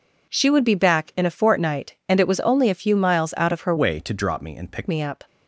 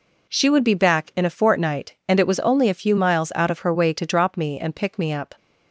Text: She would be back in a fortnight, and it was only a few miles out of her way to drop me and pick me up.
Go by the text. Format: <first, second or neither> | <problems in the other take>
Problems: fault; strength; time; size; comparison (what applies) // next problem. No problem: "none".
second | changes voice from "way" to "pick"; from 3.7 to 4.8 s; 1.1 s long